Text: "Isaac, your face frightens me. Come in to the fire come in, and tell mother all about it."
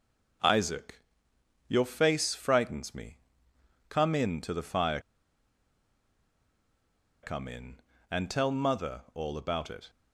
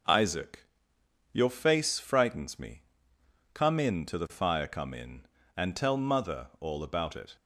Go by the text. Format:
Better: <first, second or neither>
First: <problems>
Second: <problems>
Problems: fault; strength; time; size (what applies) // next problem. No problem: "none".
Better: second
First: pauses between "fire" and "come"; strong; at 4.9 s; 2.2 s long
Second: none